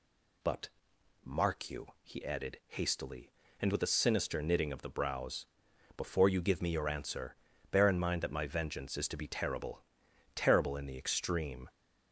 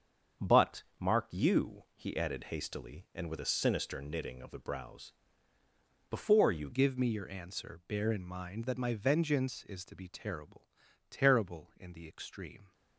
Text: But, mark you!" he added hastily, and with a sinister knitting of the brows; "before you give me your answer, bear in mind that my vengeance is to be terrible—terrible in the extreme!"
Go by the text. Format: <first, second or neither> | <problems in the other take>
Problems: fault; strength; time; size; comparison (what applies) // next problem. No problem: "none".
first | starts louder than the rest; strong; until 1.6 s; 7.5 dB // changes voice at "give"; from 6.7 s on; 6.0 s long